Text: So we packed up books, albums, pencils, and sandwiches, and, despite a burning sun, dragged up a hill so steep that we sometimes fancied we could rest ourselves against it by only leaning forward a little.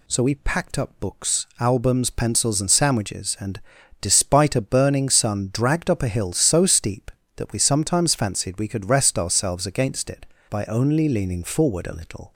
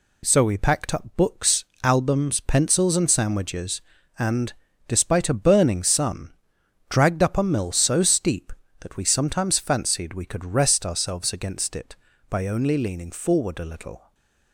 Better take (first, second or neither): first